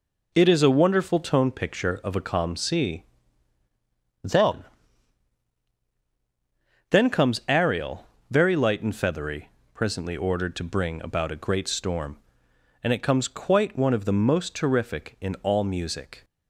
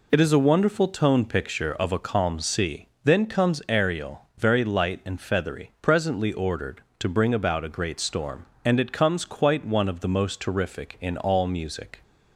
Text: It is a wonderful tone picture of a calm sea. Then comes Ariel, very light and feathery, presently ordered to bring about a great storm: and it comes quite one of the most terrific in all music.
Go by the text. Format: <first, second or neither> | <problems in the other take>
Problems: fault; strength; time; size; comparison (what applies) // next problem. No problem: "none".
second | says "Then" twice; at 6.8 s